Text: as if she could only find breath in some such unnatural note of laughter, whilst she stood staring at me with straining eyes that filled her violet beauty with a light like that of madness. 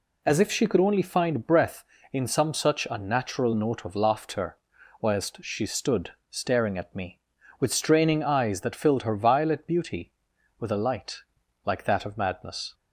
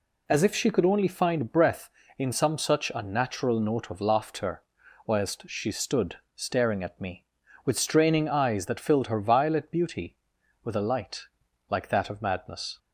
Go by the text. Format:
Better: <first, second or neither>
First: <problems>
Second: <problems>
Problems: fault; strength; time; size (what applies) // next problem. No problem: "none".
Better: neither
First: pauses between "stood" and "staring"; slight; at 6.0 s; 0.20 s long // pauses between "light" and "like"; noticeable; at 11.1 s; 0.46 s long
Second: pauses between "stood" and "staring"; slight; at 6.1 s; 0.20 s long // pauses between "light" and "like"; noticeable; at 11.2 s; 0.46 s long